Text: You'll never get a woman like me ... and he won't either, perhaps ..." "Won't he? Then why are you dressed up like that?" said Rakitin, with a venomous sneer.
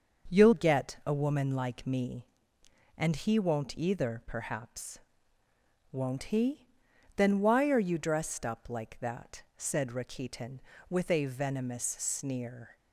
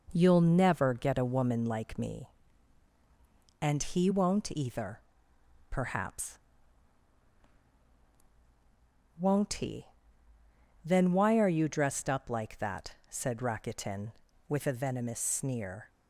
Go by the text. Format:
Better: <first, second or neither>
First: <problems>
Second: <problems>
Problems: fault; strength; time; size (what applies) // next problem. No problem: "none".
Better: second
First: starts louder than the rest; until 1.3 s; 6.5 dB // skips "never"; at 0.5 s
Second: none